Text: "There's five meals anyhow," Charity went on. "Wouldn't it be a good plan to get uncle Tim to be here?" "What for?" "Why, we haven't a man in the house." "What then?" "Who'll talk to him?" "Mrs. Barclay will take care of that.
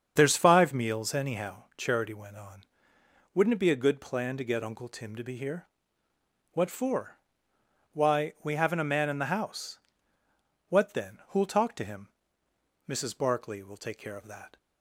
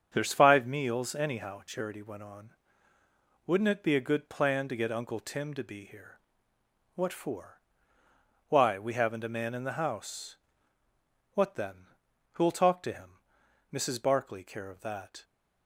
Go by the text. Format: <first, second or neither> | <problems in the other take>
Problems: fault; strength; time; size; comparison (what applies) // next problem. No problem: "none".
first | starts louder than the rest; strong; until 1.1 s; 7.5 dB; strong in the first // skips "will take"; at 14.4 s